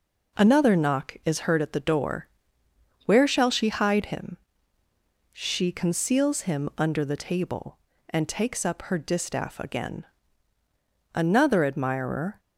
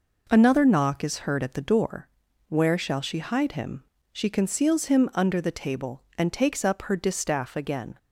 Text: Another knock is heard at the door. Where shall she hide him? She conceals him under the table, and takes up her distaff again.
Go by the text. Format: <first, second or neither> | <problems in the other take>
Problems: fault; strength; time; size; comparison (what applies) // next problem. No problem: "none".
second | goes on to say "Another admirer"; noticeable; from 11.1 s on; 1.2 s long